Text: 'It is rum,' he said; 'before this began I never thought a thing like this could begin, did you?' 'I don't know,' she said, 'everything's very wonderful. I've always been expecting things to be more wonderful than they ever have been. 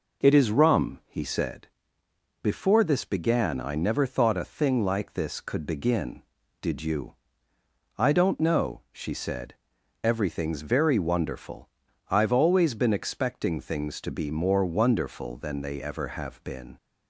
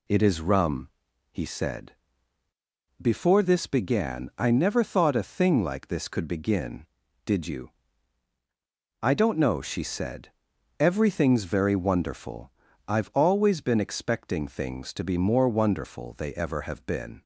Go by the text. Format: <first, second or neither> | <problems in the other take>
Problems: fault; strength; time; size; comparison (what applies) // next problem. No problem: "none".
first | skips "than"; at 16.1 s